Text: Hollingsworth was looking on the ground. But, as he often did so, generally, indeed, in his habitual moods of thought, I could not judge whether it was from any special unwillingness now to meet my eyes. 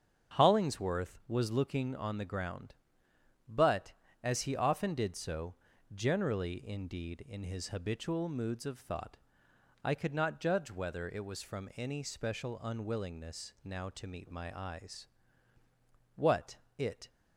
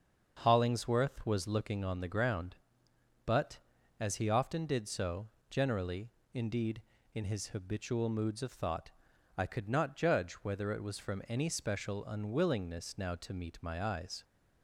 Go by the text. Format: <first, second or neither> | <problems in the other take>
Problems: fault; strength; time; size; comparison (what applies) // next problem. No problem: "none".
second | starts louder than the rest; strong; until 1.4 s; 7.5 dB; also in the second // goes on to say "What it"; noticeable; from 16.1 s on; 0.94 s long